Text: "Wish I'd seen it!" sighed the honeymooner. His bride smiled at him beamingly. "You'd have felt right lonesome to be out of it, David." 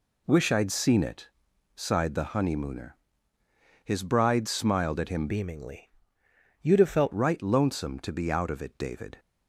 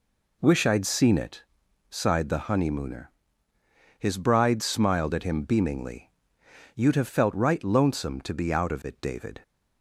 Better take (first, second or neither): second